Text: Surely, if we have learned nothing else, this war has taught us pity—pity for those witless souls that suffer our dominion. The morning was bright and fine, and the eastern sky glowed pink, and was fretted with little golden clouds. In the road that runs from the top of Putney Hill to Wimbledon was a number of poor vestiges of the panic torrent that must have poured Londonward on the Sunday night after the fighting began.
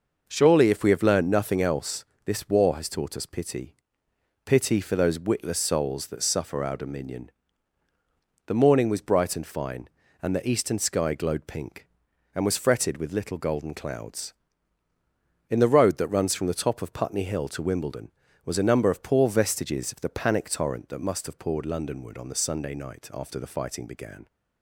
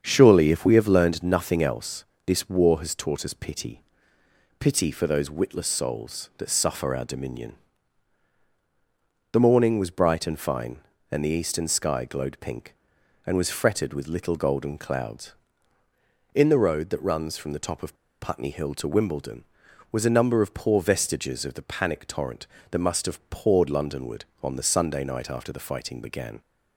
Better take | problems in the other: first | starts louder than the rest; strong; until 1.0 s; 7.5 dB // pauses between "of" and "Putney"; slight; at 17.9 s; 0.26 s long

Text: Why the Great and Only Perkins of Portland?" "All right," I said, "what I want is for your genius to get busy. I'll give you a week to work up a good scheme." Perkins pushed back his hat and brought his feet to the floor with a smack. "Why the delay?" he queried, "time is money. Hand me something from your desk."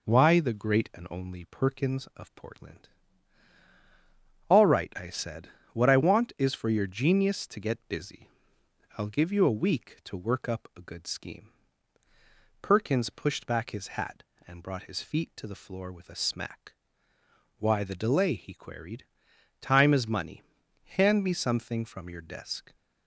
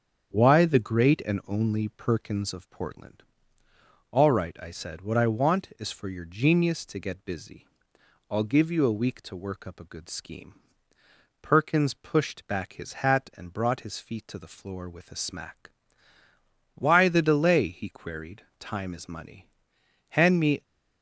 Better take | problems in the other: first | starts louder than the rest; strong; until 1.4 s; 7.5 dB // stops before "something from your desk"; at 20.6 s

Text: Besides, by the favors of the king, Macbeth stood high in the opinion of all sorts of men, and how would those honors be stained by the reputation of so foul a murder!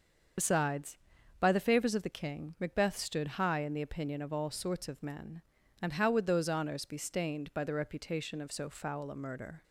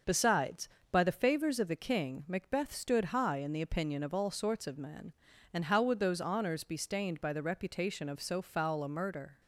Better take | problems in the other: second | loses the start of "Besides"; at 0.3 s; 60 ms // starts louder than the rest; until 1.8 s; 7 dB; noticeable in the second

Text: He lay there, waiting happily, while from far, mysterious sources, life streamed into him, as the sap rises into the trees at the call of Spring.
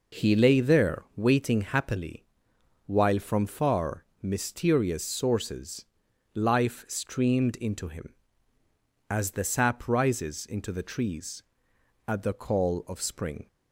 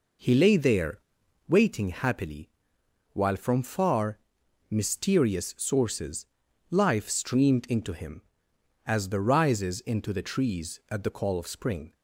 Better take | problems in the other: first | skips "sap"; at 9.2 s

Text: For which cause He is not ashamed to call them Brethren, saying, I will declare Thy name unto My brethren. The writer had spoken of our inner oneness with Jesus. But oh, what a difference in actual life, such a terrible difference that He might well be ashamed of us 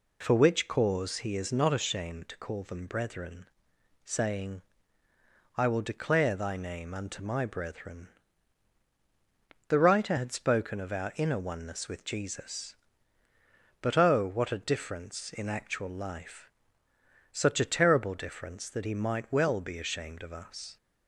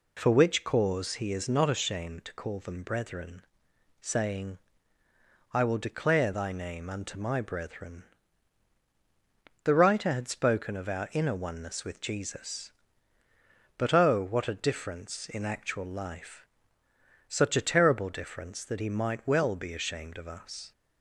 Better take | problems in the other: neither | none

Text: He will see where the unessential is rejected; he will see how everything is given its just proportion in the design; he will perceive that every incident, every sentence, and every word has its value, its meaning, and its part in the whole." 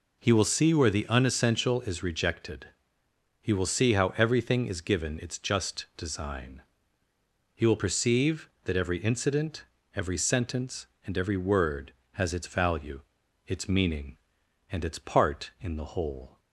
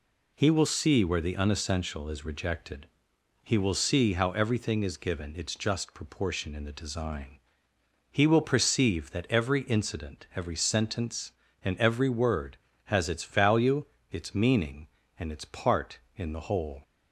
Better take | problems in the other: second | skips "proportion in the"; at 5.9 s

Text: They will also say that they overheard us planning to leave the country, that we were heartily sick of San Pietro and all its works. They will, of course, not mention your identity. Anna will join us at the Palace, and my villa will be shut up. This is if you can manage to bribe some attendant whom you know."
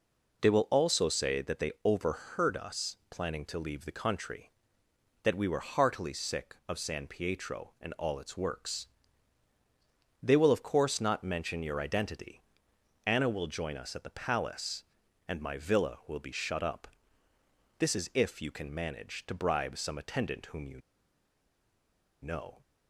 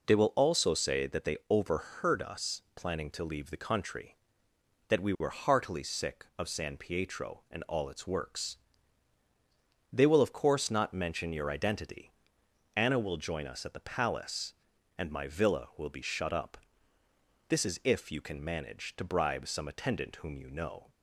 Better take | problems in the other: second | pauses between "you" and "know"; strong; at 20.7 s; 1.4 s long

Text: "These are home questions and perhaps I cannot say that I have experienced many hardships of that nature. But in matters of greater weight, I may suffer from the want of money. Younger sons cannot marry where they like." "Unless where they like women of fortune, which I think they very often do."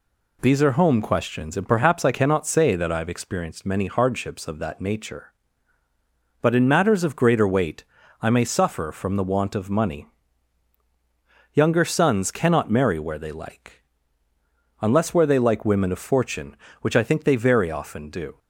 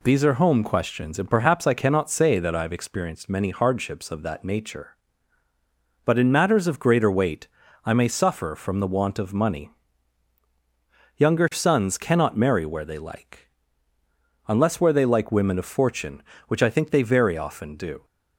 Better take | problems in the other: neither | none

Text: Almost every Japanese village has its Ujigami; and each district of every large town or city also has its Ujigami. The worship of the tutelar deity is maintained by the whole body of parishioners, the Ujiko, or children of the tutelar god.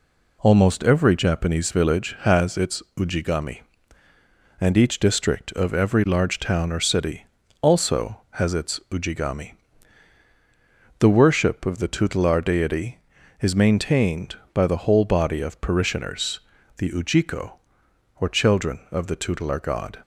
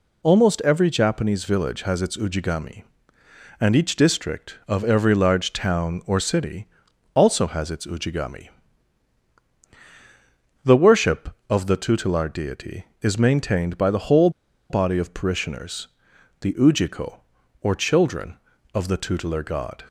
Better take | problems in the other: first | pauses between "city" and "also"; noticeable; at 6.6 s; 0.48 s long; slight in the first // pauses between "whole" and "body"; at 14.2 s; 0.40 s long

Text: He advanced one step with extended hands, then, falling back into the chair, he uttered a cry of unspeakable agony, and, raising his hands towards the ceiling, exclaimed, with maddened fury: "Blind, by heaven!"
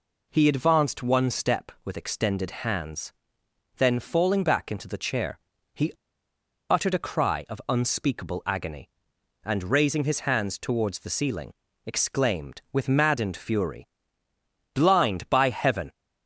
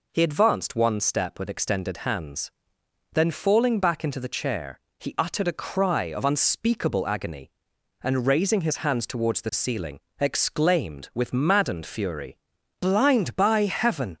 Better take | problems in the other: second | pauses between "he" and "uttered"; noticeable; at 5.9 s; 0.76 s long

